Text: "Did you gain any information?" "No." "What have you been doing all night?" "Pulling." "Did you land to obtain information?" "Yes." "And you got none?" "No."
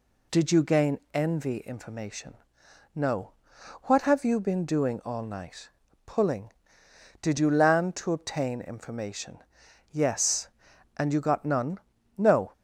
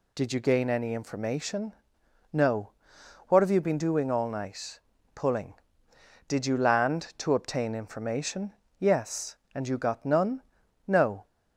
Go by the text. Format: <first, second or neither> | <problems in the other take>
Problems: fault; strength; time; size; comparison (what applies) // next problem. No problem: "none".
second | says "envy" for "any"; at 1.1 s